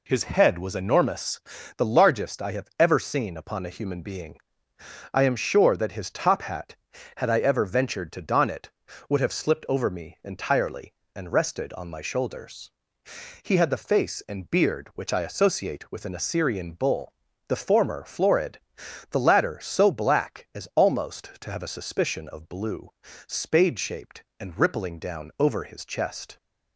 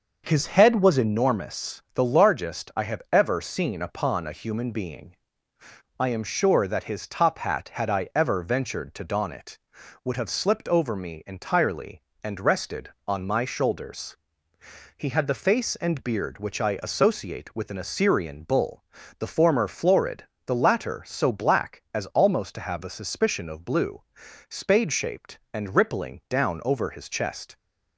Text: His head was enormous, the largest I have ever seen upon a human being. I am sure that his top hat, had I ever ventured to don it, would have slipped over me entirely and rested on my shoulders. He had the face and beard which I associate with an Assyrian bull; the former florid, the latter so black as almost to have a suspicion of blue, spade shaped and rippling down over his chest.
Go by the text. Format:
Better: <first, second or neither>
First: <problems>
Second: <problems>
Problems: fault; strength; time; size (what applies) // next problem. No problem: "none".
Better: first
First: none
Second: starts louder than the rest; noticeable; until 1.2 s; 6 dB